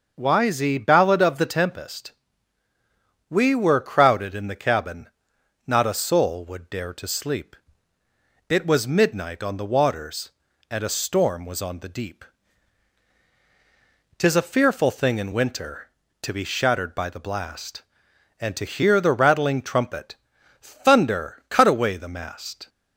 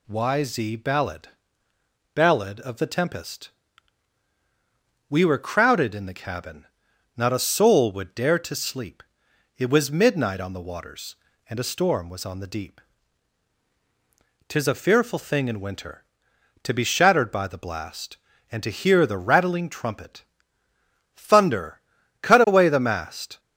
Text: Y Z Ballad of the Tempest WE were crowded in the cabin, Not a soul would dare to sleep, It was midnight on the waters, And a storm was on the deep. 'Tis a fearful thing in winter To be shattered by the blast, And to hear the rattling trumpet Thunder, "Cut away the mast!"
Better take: first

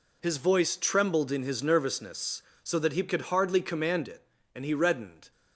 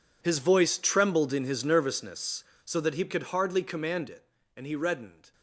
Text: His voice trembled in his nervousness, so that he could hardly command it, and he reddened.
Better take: first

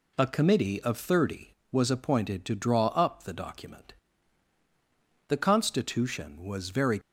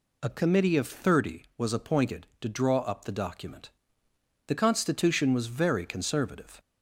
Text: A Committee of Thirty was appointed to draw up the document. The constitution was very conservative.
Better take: second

